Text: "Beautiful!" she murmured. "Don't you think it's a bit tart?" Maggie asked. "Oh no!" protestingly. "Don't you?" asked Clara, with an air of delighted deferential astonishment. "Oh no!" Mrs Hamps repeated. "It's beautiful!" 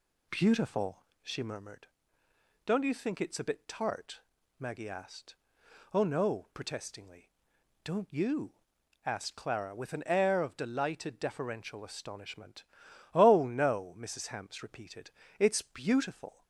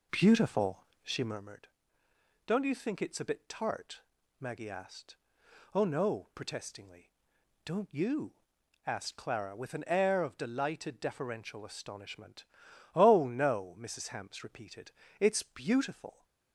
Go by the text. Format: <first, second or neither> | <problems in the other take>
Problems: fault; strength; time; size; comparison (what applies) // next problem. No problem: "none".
first | starts louder than the rest; until 1.5 s; 3.5 dB